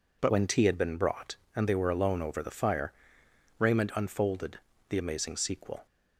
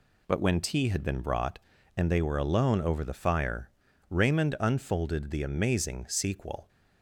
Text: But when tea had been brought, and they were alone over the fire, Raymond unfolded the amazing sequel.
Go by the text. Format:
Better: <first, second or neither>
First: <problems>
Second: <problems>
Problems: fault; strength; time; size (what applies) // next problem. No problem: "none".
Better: second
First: changes voice at "when"; from 0.2 s on; 5.6 s long // pauses between "unfolded" and "the"; slight; at 4.5 s; 0.32 s long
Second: none